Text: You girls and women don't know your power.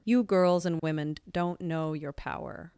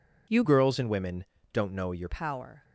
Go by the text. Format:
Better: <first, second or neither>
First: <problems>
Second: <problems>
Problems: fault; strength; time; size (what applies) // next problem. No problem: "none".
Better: first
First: none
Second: changes voice from "girls" to "your"; from 0.4 to 2.0 s; 1.6 s long // pauses between "women" and "don't"; slight; at 1.2 s; 0.26 s long